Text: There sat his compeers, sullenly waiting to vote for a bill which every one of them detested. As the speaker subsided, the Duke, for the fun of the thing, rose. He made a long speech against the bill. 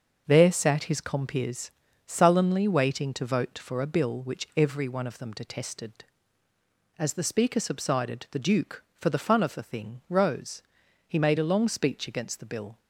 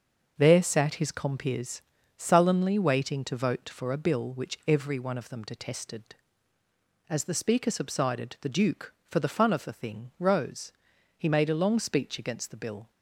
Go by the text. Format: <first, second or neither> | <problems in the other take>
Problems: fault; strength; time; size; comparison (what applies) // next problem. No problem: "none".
neither | starts louder than the rest; the same in both